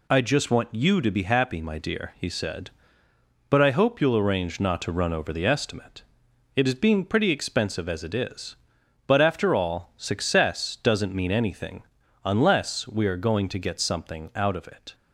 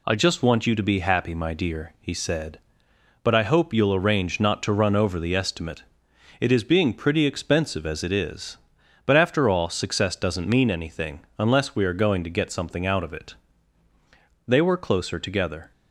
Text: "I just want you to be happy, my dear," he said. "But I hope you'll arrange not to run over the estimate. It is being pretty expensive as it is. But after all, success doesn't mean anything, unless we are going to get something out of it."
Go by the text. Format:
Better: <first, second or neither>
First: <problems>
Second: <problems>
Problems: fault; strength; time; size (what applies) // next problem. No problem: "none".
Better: first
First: none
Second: goes on to say "They were closer together"; noticeable; from 14.4 s on; 1.2 s long